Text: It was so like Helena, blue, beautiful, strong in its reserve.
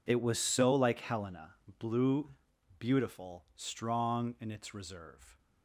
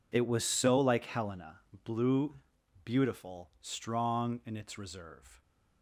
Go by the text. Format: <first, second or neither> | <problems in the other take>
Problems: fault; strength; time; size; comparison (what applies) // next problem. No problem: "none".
neither | none